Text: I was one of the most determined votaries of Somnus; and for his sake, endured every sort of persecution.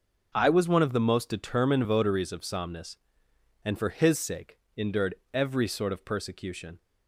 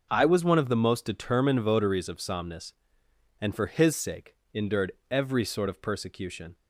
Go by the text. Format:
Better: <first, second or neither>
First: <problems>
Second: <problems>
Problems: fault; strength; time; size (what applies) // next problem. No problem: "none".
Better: neither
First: pauses between "endured" and "every"; slight; at 5.1 s; 0.18 s long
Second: pauses between "endured" and "every"; slight; at 4.9 s; 0.18 s long